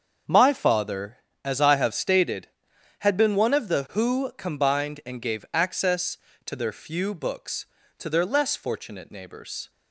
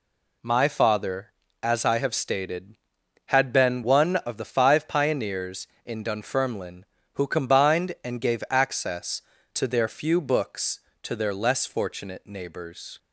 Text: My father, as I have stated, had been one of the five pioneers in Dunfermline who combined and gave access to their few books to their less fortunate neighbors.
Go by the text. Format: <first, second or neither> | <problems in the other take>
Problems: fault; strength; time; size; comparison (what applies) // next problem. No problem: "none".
second | starts louder than the rest; until 1.5 s; 7 dB // skips "five pioneers in Dunfermline"; at 3.8 s